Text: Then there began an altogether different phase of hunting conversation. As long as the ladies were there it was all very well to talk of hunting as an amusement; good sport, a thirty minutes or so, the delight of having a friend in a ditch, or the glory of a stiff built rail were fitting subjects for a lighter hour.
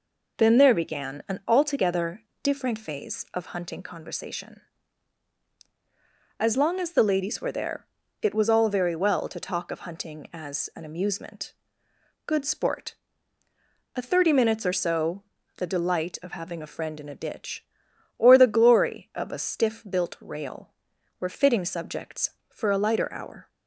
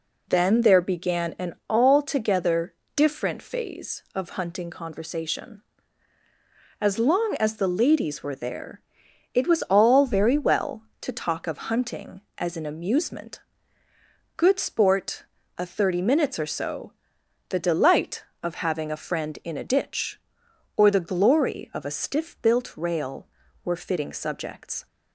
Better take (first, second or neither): first